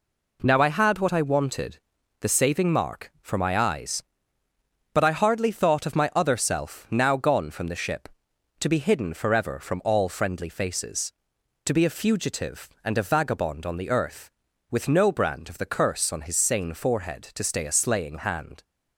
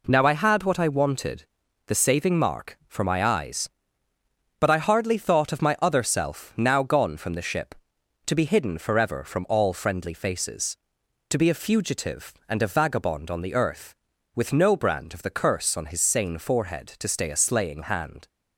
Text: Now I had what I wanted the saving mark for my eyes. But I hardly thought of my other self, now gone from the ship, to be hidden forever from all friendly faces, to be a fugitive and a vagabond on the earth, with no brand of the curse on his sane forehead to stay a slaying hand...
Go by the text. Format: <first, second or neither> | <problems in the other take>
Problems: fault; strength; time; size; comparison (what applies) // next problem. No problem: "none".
neither | pauses between "wanted" and "the"; the same in both